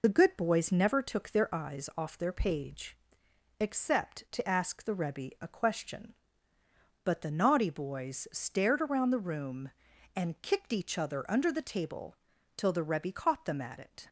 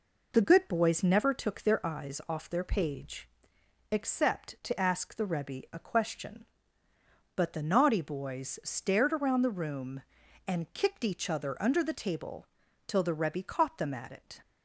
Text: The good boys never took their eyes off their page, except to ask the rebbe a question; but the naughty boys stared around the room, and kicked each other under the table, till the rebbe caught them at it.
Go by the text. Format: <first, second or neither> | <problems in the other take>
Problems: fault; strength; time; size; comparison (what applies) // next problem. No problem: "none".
second | loses the start of "The"; at 0.0 s; 30 ms